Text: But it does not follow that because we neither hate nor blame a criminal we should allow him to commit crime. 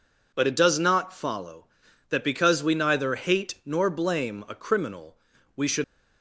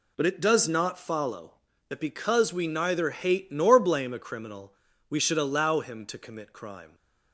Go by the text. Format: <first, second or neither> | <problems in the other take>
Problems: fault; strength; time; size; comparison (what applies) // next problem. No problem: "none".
second | pauses between "criminal" and "we"; at 5.1 s; 0.40 s long; slight in the second // stops before "allow him to commit crime"; at 5.8 s